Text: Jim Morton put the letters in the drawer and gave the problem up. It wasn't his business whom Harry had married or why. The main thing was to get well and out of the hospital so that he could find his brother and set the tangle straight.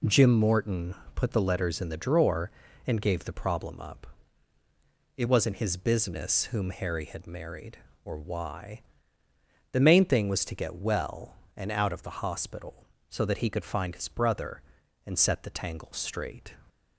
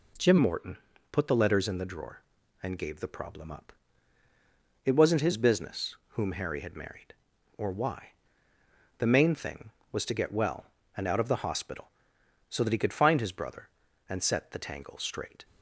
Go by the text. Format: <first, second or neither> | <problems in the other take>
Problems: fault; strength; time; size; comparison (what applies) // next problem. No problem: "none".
first | changes voice at "Morton"; from 0.3 s on; 15.1 s long // pauses between "Morton" and "put"; slight; at 0.7 s; 0.36 s long; slight in the first // pauses between "business" and "whom"; slight; at 5.9 s; 0.20 s long